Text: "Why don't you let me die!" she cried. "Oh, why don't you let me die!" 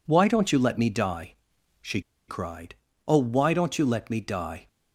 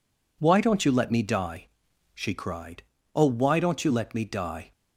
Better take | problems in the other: second | pauses between "she" and "cried"; slight; at 2.0 s; 0.27 s long

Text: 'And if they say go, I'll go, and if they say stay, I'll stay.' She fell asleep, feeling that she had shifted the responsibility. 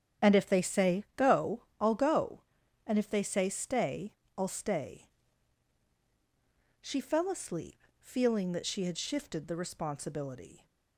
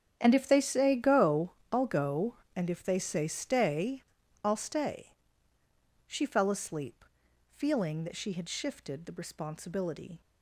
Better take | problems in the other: first | gets quieter; strong; throughout; 15 dB // starts louder than the rest; strong; until 1.2 s; 8.5 dB; strong in the first

